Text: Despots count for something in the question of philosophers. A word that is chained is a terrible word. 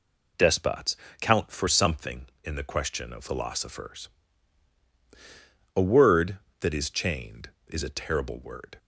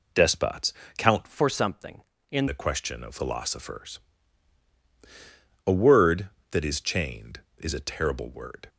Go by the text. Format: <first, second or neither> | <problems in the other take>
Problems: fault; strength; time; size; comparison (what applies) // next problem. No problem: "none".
first | pauses between "Despots" and "count"; slight; at 0.7 s; 0.24 s long; slight in the first // changes voice from "for" to "in"; from 1.2 to 2.4 s; 1.2 s long